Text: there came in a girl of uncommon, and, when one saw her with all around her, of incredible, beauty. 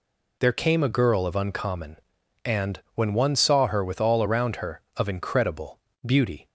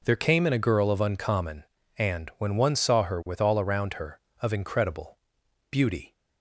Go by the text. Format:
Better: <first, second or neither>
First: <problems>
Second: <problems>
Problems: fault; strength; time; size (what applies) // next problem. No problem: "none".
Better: second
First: skips "in"; at 0.8 s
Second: none